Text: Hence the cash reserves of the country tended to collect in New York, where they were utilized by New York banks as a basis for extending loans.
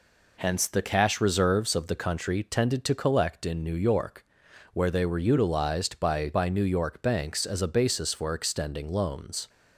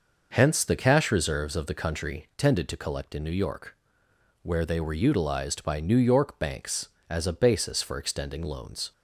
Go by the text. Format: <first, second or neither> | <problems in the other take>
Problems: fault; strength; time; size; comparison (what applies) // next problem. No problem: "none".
second | says "by" twice; at 6.3 s